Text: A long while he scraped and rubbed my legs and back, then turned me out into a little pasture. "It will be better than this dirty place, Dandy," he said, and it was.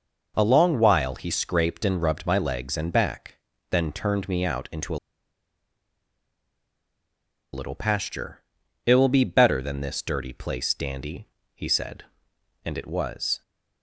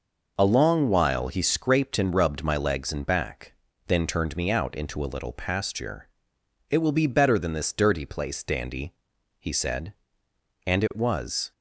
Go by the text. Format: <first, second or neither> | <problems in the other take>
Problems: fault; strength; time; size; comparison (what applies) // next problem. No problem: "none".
second | pauses between "a" and "little"; strong; at 4.9 s; 2.5 s long